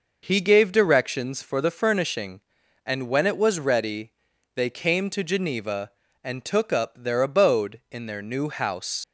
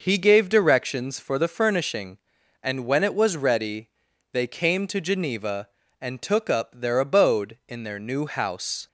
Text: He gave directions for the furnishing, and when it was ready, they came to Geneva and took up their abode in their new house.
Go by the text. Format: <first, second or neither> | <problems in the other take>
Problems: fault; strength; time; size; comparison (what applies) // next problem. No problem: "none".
second | leaves "house" unfinished; at 9.0 s; 60 ms